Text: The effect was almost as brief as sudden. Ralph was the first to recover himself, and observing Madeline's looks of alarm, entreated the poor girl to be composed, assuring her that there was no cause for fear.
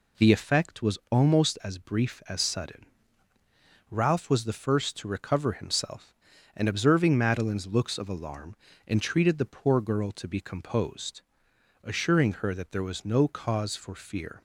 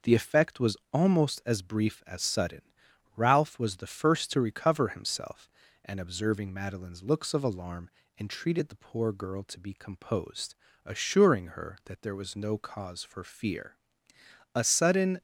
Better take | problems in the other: first | pauses between "was" and "almost"; slight; at 0.7 s; 0.16 s long // goes on to say "A sudden"; noticeable; from 14.5 s on; 0.66 s long

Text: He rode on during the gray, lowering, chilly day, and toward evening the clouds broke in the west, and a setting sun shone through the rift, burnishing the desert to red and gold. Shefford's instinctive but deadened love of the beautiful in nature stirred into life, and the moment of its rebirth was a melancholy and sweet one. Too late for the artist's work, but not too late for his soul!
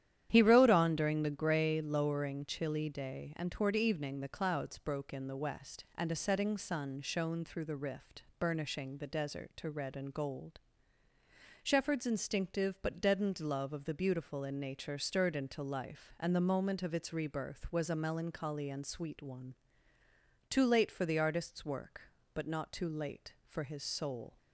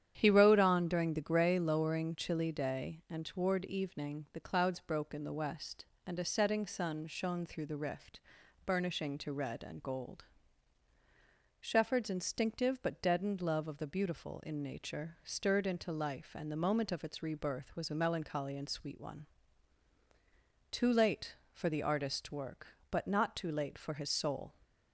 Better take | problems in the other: first | starts louder than the rest; strong; until 1.1 s; 9.5 dB; strong in the first // skips "the desert"; at 9.1 s

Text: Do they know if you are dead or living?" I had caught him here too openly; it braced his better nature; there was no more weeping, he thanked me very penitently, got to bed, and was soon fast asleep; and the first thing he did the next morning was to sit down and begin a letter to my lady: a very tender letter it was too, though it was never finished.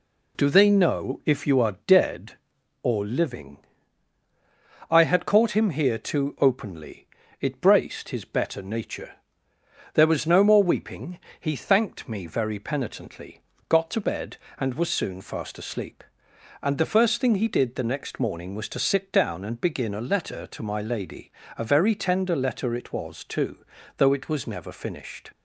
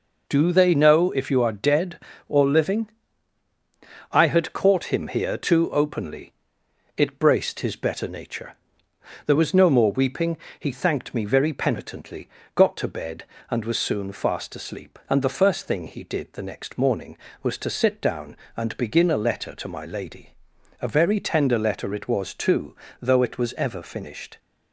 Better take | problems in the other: first | says "ever" for "never"; at 23.5 s

